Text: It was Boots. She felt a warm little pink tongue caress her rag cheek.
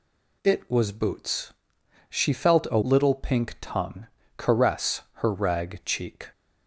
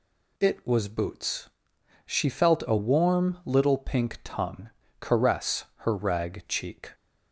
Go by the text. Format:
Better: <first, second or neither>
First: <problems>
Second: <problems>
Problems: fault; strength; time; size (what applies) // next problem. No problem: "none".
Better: second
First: skips "warm"; at 2.8 s // pauses between "tongue" and "caress"; slight; at 4.0 s; 0.28 s long // pauses between "caress" and "her"; slight; at 5.0 s; 0.16 s long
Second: pauses between "tongue" and "caress"; slight; at 4.7 s; 0.28 s long // pauses between "caress" and "her"; slight; at 5.6 s; 0.16 s long